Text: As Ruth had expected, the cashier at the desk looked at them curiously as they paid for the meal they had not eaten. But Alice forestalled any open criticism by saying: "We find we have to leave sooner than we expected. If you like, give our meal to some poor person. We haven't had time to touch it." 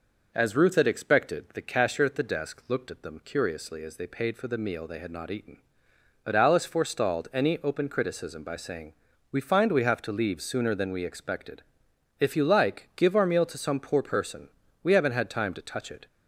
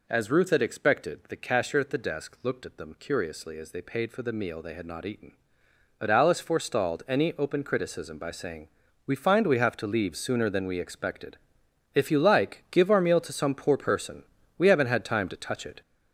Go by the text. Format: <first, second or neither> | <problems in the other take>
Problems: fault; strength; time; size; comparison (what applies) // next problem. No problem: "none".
first | gets louder; noticeable; throughout; 5.5 dB